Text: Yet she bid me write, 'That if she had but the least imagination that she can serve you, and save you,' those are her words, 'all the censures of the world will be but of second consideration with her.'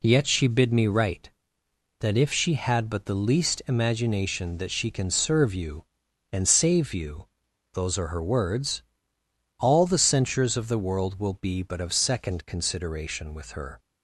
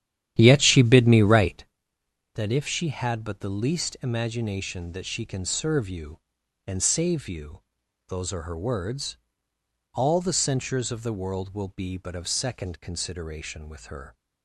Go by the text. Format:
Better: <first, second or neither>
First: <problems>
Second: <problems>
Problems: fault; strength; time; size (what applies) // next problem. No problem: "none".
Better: first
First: none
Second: starts louder than the rest; strong; until 1.7 s; 11 dB